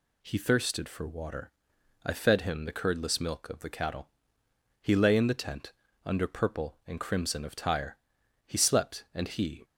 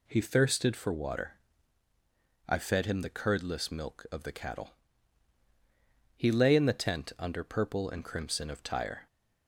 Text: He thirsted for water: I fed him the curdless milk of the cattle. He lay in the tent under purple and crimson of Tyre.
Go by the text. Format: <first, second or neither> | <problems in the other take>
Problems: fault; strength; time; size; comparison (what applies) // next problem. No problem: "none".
second | pauses between "tent" and "under"; slight; at 5.7 s; 0.32 s long // goes on to say "He slept and he"; noticeable; from 8.4 s on; 1.1 s long